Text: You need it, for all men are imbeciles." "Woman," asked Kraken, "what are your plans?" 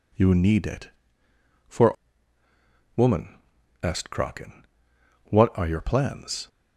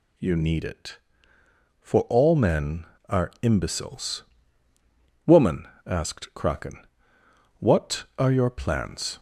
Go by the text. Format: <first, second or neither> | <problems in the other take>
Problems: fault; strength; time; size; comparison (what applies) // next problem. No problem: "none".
second | skips "all men are imbeciles"; at 2.4 s